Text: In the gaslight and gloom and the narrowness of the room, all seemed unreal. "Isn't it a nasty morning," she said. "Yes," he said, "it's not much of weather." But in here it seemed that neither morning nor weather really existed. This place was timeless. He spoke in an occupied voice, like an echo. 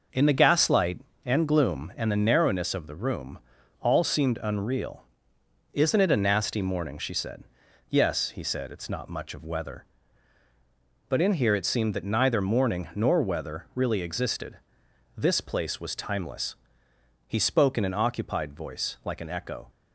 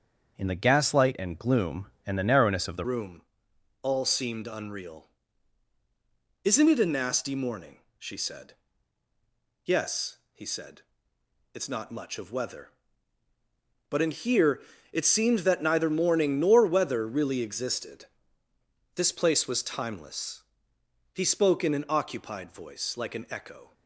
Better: first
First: none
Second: starts louder than the rest; until 1.4 s; 7 dB // changes voice at "room"; from 2.8 s on; 20.9 s long // pauses between "here" and "it"; slight; at 14.6 s; 0.30 s long

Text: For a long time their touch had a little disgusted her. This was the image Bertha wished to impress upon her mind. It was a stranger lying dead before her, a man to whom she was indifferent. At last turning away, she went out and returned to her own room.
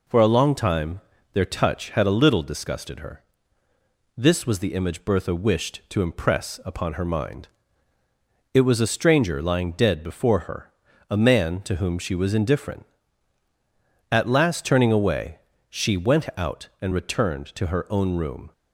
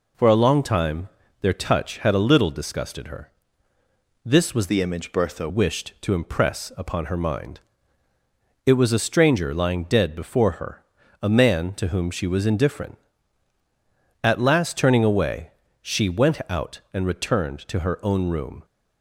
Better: first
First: pauses between "time" and "their"; slight; at 1.0 s; 0.32 s long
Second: pauses between "time" and "their"; slight; at 1.0 s; 0.32 s long // changes voice from "the" to "Bertha"; from 4.6 to 5.4 s; 0.8 s long

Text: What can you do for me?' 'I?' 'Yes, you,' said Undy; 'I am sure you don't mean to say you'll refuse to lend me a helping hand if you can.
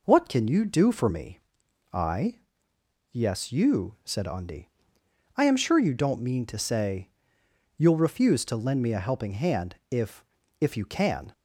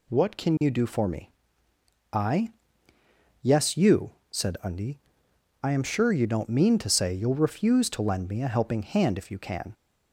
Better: second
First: pauses between "say" and "you'll"; noticeable; at 7.0 s; 0.70 s long // says "if" twice; at 10.6 s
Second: none

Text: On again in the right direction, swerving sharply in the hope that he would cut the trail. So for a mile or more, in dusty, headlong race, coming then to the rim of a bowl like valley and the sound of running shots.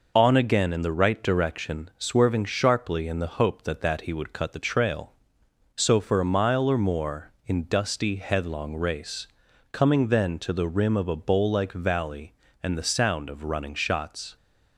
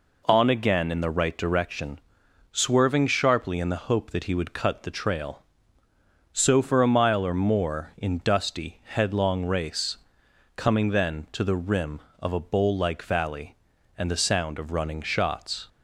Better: second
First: says "that" twice; at 3.8 s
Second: none

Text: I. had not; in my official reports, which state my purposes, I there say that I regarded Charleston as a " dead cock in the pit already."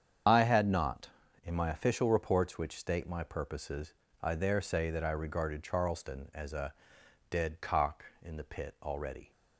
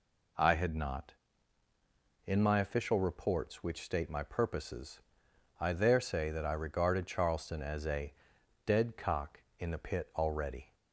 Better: second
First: loses the start of "I"; at 0.2 s; 30 ms // starts louder than the rest; strong; until 1.6 s; 8 dB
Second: none

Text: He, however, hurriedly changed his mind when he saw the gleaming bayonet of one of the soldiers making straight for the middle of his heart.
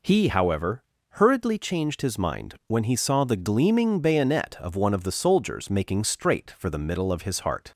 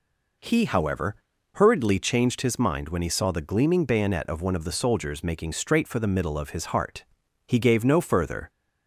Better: first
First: none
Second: goes on to say "He gave no further"; noticeable; from 7.4 s on; 1.0 s long

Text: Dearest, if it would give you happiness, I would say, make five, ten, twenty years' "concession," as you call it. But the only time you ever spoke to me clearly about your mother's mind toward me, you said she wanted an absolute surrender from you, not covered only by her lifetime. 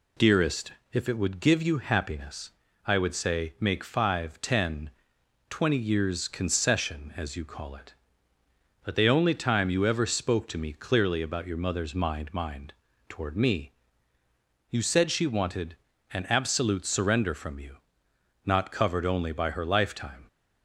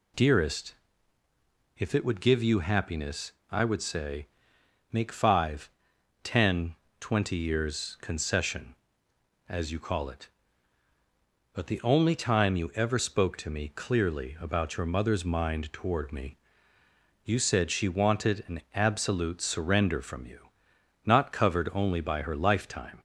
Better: second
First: says "mind" twice; at 12.3 s // pauses between "wanted" and "an"; slight; at 15.7 s; 0.36 s long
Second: none

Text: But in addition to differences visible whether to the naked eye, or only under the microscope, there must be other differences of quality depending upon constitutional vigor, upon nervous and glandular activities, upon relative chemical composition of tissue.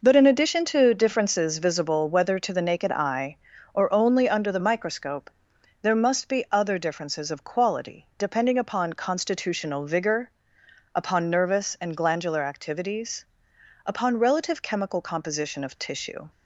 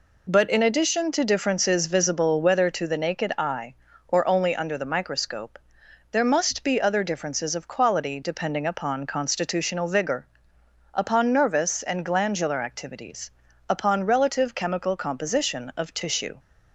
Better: second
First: starts louder than the rest; noticeable; until 1.5 s; 5 dB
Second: none

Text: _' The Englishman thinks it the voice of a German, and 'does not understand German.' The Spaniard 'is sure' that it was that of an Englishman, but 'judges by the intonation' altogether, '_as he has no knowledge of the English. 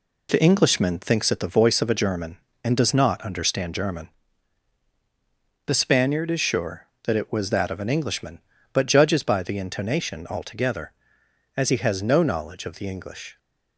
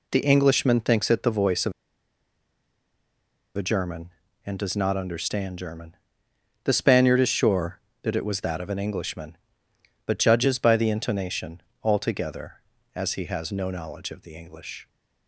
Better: first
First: none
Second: pauses between "of" and "a"; strong; at 1.7 s; 1.8 s long // pauses between "intonation" and "altogether"; slight; at 11.6 s; 0.22 s long

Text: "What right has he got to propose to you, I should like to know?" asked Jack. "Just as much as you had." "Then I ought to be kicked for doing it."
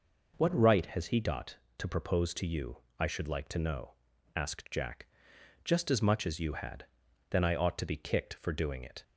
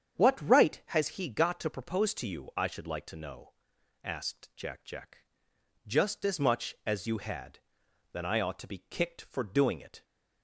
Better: first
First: none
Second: starts louder than the rest; strong; until 1.2 s; 8 dB // says "Jack" twice; at 4.8 s

